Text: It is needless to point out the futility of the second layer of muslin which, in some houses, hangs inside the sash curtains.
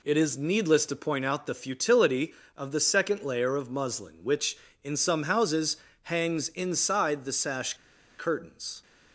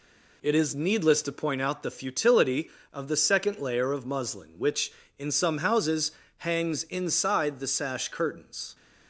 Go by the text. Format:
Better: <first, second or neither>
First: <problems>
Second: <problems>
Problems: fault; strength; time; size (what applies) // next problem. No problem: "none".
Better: second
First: pauses between "sash" and "curtains"; at 7.7 s; 0.44 s long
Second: none